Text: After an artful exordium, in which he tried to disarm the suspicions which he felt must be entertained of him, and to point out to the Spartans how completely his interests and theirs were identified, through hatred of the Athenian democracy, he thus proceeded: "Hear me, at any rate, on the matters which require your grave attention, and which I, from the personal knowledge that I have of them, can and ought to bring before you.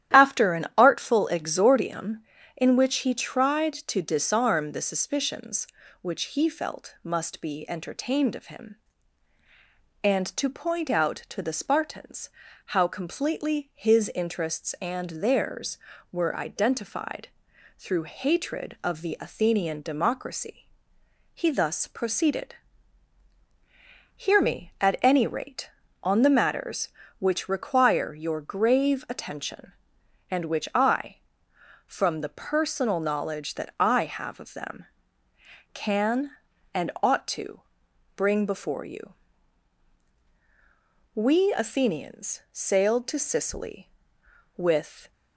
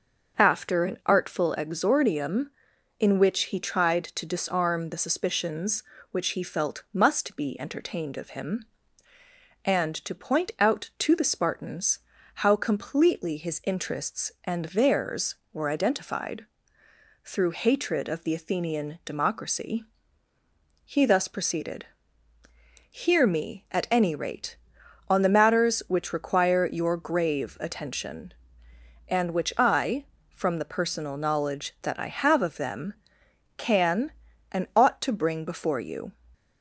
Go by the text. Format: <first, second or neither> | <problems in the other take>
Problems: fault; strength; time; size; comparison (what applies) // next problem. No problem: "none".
second | starts louder than the rest; strong; until 1.2 s; 12 dB; also in the second // pauses between "Spartans" and "how"; at 12.2 s; 0.38 s long; slight in the second // pauses between "to" and "bring"; noticeable; at 37.6 s; 0.54 s long // goes on to say "We Athenians sailed to Sicily with"; strong; from 41.1 s on; 3.9 s long